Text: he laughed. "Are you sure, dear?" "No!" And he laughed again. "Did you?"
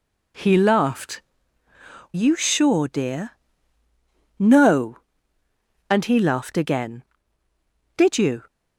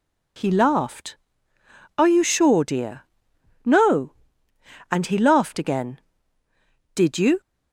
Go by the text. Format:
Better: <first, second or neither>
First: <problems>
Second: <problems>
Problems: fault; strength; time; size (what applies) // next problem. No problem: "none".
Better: second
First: skips "Are"; at 1.6 s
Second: none